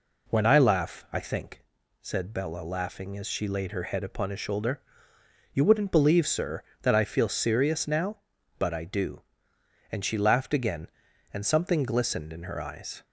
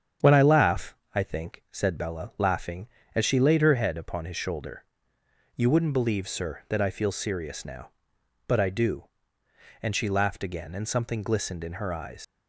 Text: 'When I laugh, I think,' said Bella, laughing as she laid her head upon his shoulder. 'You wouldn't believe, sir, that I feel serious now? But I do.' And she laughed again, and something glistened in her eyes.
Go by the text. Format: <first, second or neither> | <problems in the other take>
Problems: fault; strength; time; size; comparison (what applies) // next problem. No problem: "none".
first | starts louder than the rest; strong; until 1.4 s; 8.5 dB // leaves "eyes" unfinished; at 12.2 s; 105 ms